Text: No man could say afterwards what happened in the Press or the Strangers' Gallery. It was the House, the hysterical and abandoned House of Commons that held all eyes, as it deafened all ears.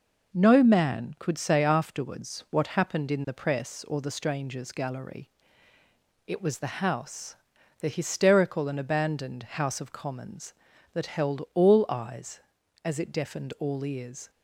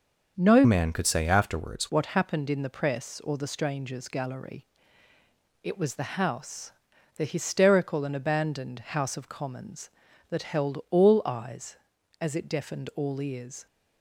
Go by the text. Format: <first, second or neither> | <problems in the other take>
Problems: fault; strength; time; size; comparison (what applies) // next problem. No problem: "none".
first | starts louder than the rest; until 1.3 s; 6 dB // changes voice from "man" to "afterwards"; from 0.6 to 1.8 s; 1.2 s long